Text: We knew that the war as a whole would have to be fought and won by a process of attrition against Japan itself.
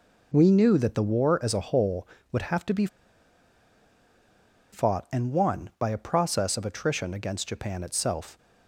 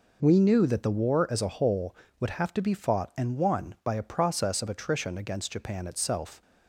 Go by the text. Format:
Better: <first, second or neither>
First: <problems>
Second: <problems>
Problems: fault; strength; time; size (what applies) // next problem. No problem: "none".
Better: second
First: pauses between "be" and "fought"; strong; at 2.8 s; 1.8 s long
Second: none